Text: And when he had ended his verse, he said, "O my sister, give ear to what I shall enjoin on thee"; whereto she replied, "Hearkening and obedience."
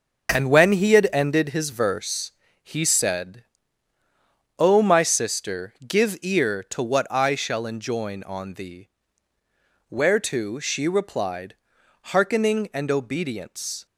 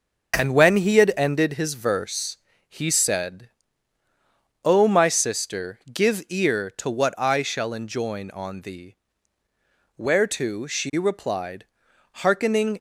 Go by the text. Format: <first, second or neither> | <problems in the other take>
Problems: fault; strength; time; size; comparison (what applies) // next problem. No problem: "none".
first | stops before "and obedience"; at 12.7 s